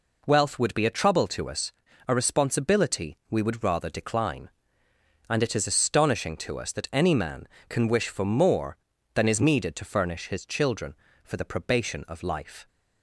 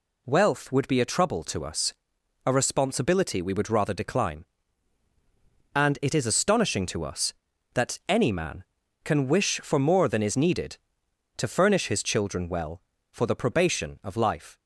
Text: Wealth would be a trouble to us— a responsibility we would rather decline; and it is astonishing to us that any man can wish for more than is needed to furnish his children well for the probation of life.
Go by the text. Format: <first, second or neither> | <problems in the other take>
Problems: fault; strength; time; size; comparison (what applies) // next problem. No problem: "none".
second | skips "well"; at 11.0 s